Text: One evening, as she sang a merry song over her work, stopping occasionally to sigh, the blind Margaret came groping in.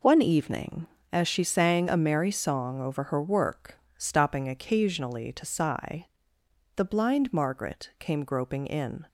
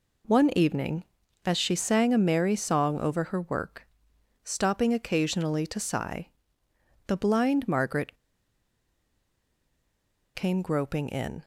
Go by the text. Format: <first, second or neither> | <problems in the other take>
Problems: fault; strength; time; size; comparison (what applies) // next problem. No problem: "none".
first | pauses between "Margaret" and "came"; strong; at 8.1 s; 2.1 s long